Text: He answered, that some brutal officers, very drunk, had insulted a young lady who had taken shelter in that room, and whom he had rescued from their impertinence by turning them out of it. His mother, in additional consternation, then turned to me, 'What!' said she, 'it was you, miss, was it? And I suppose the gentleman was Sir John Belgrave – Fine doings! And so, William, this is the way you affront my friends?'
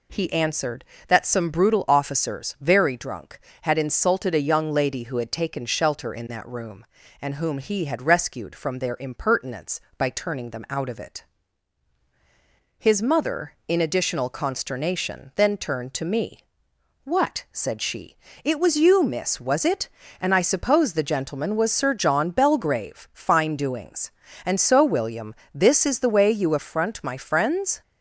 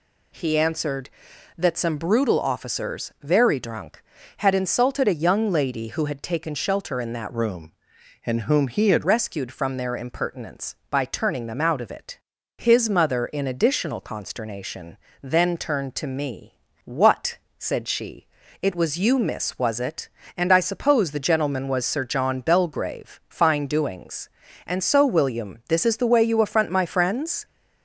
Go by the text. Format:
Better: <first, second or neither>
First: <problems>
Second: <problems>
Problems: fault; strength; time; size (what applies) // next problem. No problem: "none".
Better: first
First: none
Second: changes voice from "room" to "had"; from 7.3 to 9.0 s; 1.7 s long